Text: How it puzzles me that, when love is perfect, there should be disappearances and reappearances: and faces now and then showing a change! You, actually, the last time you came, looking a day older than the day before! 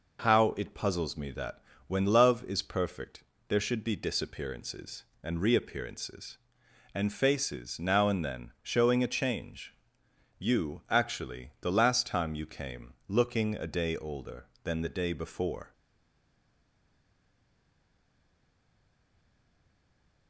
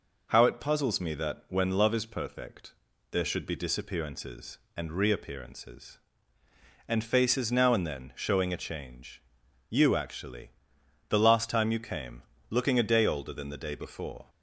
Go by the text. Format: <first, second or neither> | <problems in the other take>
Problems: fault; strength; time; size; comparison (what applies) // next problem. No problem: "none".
second | stays silent after the last word; strong; from 15.7 s on; 4.5 s long